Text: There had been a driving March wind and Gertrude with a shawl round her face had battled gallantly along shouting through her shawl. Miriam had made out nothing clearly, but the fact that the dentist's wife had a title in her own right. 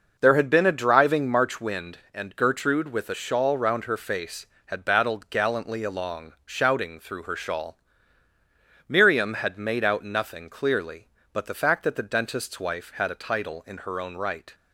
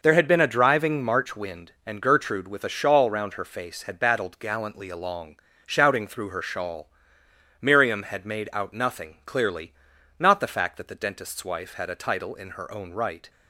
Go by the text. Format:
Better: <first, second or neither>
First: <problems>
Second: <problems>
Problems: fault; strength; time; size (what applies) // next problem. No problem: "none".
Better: first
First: none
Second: pauses between "along" and "shouting"; slight; at 5.3 s; 0.28 s long // says "not" for "but"; at 10.1 s